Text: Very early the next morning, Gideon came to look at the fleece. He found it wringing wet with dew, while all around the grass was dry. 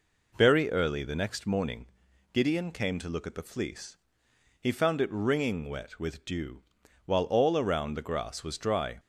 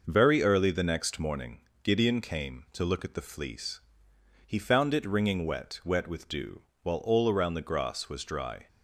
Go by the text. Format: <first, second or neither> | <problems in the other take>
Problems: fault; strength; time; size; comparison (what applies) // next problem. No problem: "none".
first | says "wet" twice; at 5.8 s